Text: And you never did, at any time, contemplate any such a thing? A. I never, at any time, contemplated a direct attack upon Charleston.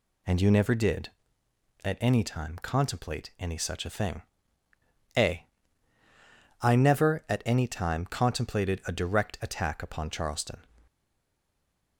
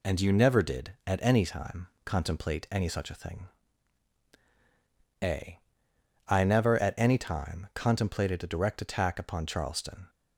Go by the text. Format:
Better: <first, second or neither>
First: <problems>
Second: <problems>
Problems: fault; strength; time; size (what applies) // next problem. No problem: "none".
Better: second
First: stays silent after the last word; from 10.8 s on; 1.1 s long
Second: none